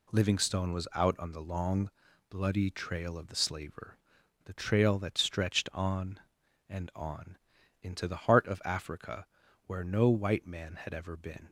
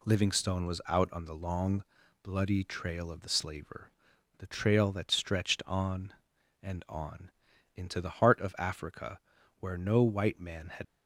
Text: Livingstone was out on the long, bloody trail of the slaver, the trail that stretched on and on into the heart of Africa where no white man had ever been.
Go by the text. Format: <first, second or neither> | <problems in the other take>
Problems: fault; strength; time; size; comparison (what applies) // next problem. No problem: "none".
first | pauses between "on" and "into"; noticeable; at 7.2 s; 0.46 s long; noticeable in the first // pauses between "Africa" and "where"; at 9.1 s; 0.40 s long; also in the first // stops before "ever been"; at 10.8 s